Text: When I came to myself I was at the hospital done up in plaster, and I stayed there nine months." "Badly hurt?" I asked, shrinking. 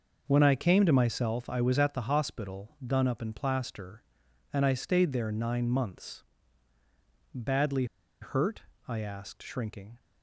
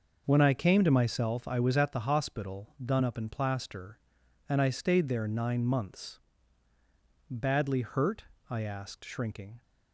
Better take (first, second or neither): second